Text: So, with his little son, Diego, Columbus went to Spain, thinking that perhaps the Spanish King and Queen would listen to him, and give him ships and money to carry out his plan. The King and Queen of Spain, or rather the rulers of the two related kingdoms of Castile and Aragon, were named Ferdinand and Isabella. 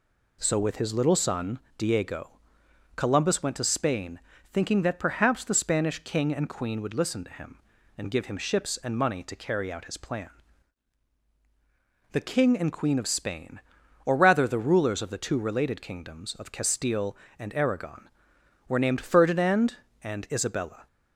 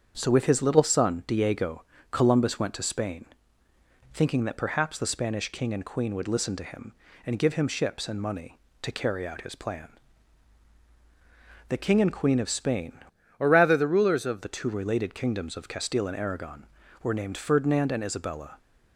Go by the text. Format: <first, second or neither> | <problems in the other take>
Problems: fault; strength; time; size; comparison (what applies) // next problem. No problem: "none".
first | starts louder than the rest; strong; until 1.1 s; 7.5 dB // changes voice from "or" to "of"; from 13.3 to 14.4 s; 1.1 s long